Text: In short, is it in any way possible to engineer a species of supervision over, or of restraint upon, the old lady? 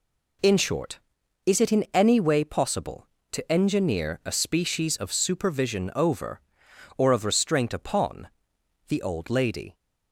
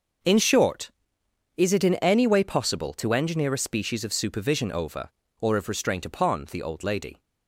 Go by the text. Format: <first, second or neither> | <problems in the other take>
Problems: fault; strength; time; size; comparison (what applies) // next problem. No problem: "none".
neither | none